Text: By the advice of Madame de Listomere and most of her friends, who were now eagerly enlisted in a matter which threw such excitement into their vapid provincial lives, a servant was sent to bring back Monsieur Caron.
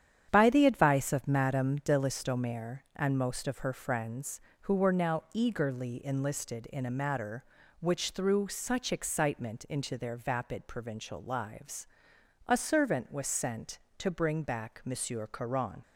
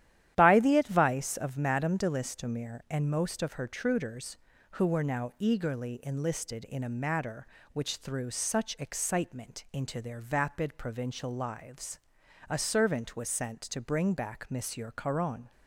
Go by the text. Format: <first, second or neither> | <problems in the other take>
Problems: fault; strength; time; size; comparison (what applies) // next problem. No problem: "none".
first | starts louder than the rest; strong; until 1.3 s; 11.5 dB; strong in the first // says "truders" for "friends"; at 3.6 s